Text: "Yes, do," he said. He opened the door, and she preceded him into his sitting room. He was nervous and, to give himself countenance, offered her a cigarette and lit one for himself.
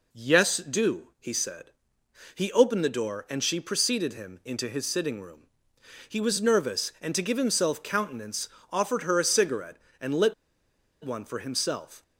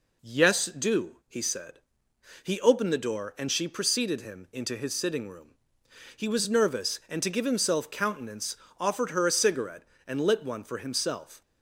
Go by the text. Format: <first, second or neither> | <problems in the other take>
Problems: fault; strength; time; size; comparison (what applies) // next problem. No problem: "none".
second | pauses between "lit" and "one"; noticeable; at 10.3 s; 0.70 s long